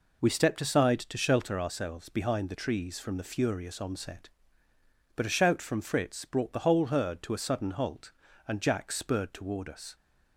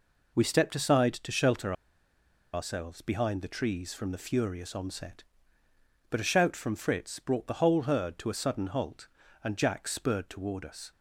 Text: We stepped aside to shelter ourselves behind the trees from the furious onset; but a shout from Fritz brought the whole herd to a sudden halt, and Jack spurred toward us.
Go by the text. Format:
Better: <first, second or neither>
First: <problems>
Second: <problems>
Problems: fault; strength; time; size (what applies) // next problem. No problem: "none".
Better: first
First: none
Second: pauses between "shelter" and "ourselves"; noticeable; at 1.7 s; 0.80 s long